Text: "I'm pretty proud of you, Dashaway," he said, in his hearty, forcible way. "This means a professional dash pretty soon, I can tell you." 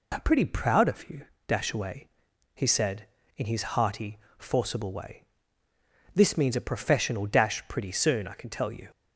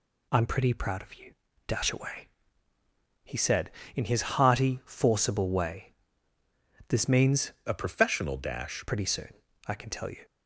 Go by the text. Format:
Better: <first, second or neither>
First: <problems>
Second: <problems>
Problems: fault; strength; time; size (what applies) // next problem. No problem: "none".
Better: first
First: none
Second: changes voice from "a" to "dash"; from 7.6 to 8.8 s; 1.2 s long